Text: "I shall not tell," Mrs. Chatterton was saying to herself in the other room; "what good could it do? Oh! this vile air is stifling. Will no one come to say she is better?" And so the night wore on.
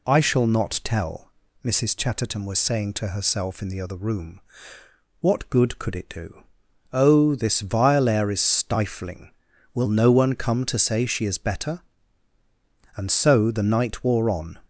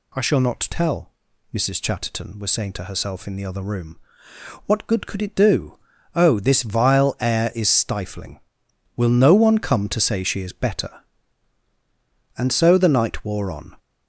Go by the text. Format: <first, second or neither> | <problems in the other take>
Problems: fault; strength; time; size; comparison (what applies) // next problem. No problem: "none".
neither | none